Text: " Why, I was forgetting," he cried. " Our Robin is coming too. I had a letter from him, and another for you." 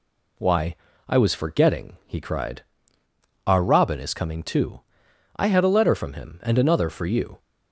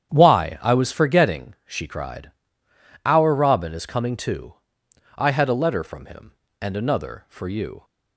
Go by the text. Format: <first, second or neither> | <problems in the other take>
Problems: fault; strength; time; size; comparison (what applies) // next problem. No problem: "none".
first | starts louder than the rest; strong; until 1.1 s; 9 dB // says "she" for "he"; at 1.6 s